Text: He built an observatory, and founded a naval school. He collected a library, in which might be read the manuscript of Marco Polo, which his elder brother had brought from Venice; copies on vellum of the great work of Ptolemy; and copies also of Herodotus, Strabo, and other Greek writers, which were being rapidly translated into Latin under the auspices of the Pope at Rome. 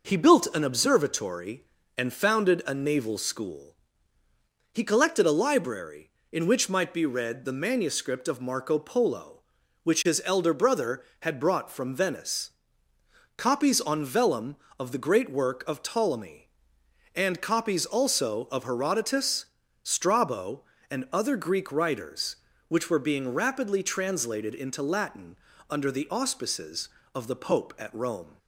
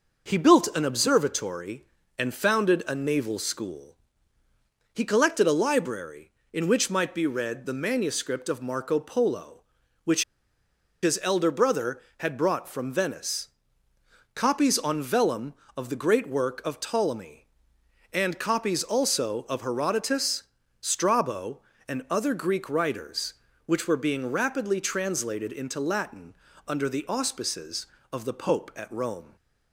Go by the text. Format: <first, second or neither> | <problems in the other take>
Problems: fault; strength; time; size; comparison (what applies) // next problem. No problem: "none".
first | pauses between "which" and "his"; noticeable; at 10.2 s; 0.80 s long // pauses between "Latin" and "under"; slight; at 26.3 s; 0.32 s long; slight in the first